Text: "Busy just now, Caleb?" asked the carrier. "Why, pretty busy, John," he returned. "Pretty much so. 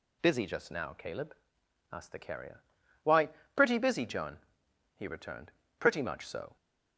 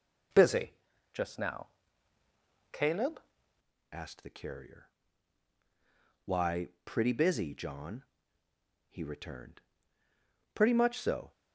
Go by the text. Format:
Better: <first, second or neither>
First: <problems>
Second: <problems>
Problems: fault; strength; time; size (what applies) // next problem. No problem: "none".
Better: first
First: none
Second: pauses between "Busy" and "just"; at 0.7 s; 0.42 s long // changes voice at "asked"; from 3.9 s on; 7.4 s long